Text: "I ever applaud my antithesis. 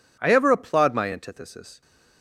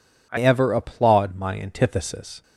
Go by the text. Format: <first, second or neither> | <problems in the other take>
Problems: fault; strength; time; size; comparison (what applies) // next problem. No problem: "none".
first | changes voice at "ever"; from 0.3 s on; 2.1 s long